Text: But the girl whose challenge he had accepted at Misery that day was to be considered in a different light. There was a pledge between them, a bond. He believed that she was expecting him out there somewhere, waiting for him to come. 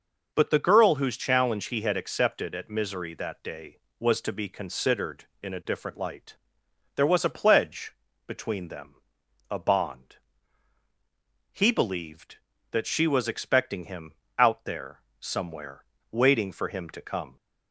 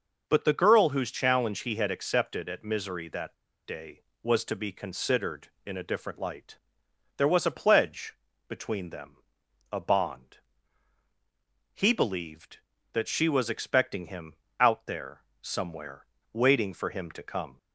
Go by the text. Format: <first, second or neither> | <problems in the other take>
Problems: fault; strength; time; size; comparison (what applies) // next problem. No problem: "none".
first | pauses between "that" and "day"; slight; at 3.3 s; 0.30 s long // pauses between "pledge" and "between"; slight; at 8.1 s; 0.32 s long; slight in the first // pauses between "him" and "out"; slight; at 14.3 s; 0.26 s long; slight in the first // pauses between "there" and "somewhere"; slight; at 15.2 s; 0.20 s long; slight in the first